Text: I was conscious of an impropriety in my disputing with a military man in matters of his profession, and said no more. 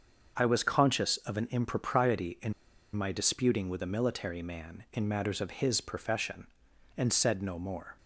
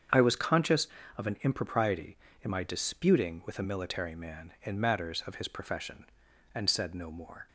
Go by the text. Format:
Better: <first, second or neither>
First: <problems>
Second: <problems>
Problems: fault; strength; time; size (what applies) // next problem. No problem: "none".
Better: second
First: starts louder than the rest; until 1.3 s; 7 dB // pauses between "in" and "my"; at 2.5 s; 0.42 s long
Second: starts louder than the rest; strong; until 1.4 s; 7.5 dB